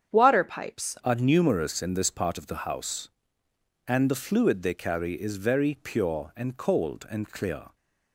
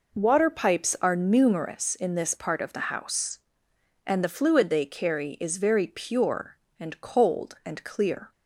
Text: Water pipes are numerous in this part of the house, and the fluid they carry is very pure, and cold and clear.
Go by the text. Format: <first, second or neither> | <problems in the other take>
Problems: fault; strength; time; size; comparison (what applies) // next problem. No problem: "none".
second | starts louder than the rest; strong; until 1.1 s; 8 dB // changes voice at "are"; from 1.0 s on; 6.7 s long